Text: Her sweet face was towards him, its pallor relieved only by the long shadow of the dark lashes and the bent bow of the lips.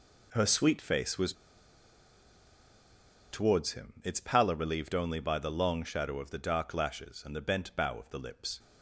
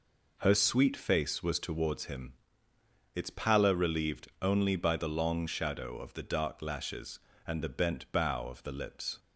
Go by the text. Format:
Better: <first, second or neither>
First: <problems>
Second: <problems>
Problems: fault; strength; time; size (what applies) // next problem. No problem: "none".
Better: second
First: pauses between "was" and "towards"; strong; at 1.3 s; 1.9 s long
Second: none